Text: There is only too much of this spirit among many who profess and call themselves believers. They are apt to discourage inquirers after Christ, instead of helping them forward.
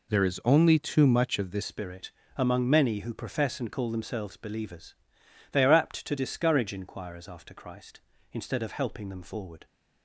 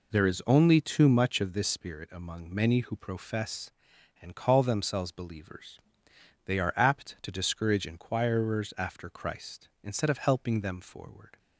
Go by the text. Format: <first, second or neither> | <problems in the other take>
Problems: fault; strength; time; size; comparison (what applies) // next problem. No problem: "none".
second | changes voice at "spirit"; from 1.6 s on; 8.0 s long // pauses between "spirit" and "among"; slight; at 2.1 s; 0.24 s long